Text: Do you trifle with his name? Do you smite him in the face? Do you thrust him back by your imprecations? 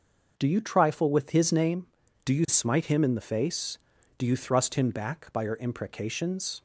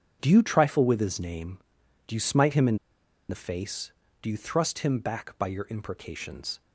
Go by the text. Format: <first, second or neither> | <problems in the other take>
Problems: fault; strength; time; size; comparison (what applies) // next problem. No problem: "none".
first | starts louder than the rest; strong; until 1.2 s; 7.5 dB; noticeable in the first // pauses between "in" and "the"; noticeable; at 2.7 s; 0.53 s long